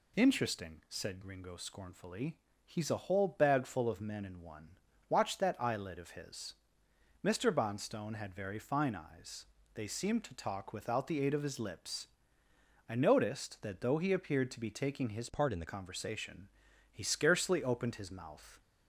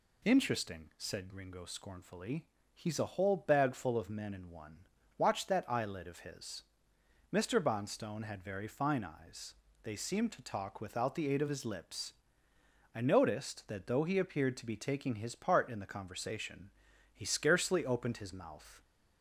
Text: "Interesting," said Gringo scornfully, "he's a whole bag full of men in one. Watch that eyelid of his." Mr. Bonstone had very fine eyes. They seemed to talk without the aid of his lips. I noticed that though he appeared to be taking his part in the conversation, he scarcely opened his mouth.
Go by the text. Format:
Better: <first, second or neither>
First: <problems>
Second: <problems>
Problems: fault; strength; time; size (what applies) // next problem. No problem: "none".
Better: second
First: changes voice from "part" to "the"; from 15.2 to 15.6 s; 0.4 s long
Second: none